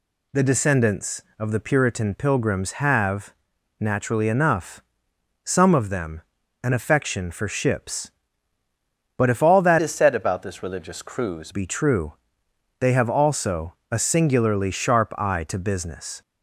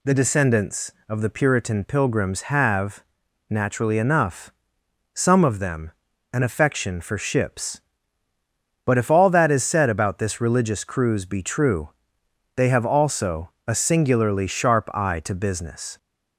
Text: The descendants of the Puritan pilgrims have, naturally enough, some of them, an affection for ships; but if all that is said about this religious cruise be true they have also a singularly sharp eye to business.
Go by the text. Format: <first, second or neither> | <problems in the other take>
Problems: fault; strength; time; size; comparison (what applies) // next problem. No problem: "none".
second | changes voice from "is" to "cruise"; from 9.8 to 11.5 s; 1.7 s long // pauses between "true" and "they"; noticeable; at 12.1 s; 0.66 s long; noticeable in the second // pauses between "also" and "a"; slight; at 13.7 s; 0.16 s long; slight in the second